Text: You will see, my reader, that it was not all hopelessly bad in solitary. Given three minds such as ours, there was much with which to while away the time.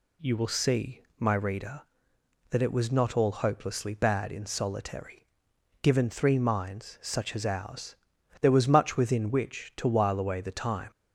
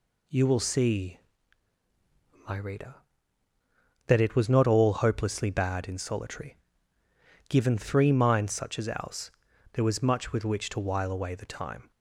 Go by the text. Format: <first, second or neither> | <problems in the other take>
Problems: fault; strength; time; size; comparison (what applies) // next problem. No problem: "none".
second | says "within" for "with"; at 8.9 s